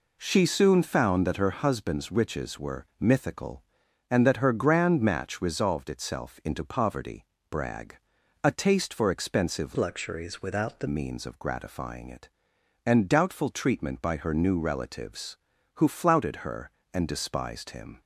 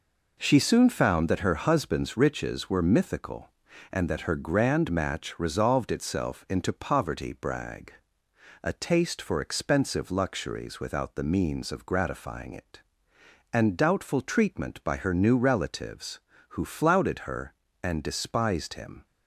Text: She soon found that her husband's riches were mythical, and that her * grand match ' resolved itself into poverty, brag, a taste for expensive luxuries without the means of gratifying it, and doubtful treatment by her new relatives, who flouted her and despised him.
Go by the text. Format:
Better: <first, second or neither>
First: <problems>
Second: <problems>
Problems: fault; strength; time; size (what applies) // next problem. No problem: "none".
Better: second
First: changes voice from "luxuries" to "the"; from 9.7 to 10.8 s; 1.1 s long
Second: none